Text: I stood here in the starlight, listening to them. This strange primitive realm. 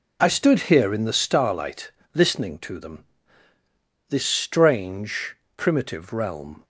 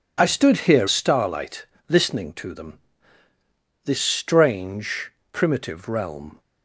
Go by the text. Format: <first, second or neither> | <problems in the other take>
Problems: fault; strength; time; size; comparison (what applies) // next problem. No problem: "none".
first | skips "in the"; at 0.8 s // pauses between "strange" and "primitive"; slight; at 5.0 s; 0.22 s long; slight in the first